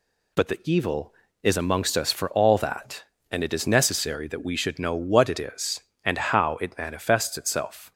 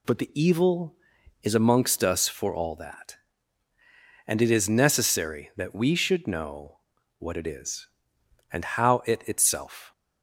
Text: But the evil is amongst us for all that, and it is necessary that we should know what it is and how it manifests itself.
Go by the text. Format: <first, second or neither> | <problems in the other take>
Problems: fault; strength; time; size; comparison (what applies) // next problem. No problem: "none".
first | pauses between "know" and "what"; at 6.7 s; 0.40 s long // skips "manifests"; at 9.2 s